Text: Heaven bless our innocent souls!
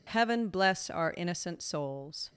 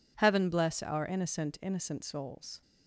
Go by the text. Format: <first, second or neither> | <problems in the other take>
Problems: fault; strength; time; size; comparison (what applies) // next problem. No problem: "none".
first | says "innocent" twice; at 1.6 s